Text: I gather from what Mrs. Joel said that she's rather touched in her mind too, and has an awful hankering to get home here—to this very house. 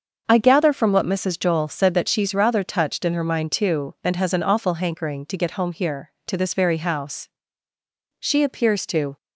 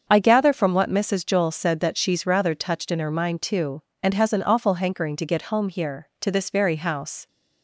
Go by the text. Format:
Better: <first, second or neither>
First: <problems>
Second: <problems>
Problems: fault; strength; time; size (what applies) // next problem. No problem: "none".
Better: second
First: starts louder than the rest; until 1.2 s; 6.5 dB // goes on to say "She appears to"; noticeable; from 8.1 s on; 0.98 s long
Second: starts louder than the rest; until 1.0 s; 7 dB